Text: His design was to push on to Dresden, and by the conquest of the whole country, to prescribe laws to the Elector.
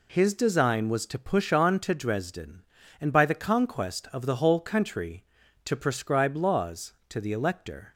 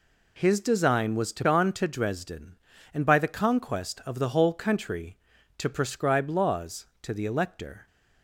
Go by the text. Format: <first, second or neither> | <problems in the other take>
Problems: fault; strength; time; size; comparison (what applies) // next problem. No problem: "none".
first | skips "push"; at 1.4 s